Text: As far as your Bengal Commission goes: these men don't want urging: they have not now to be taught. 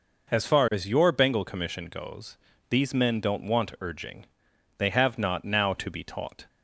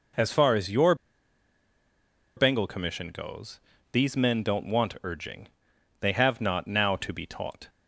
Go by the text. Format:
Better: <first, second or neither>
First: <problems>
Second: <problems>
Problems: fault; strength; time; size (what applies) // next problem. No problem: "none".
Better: first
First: none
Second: pauses between "your" and "Bengal"; strong; at 0.9 s; 1.4 s long